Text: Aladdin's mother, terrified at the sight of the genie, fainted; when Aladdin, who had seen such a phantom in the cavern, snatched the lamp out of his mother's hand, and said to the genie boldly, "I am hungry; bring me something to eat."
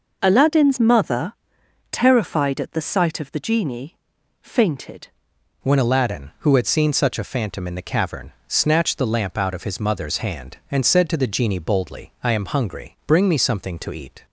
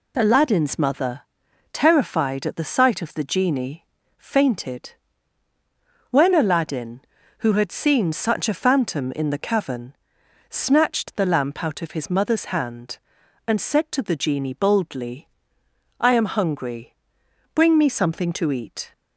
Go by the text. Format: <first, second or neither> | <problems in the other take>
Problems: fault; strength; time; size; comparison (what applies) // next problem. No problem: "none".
second | changes voice at "when"; from 5.6 s on; 8.6 s long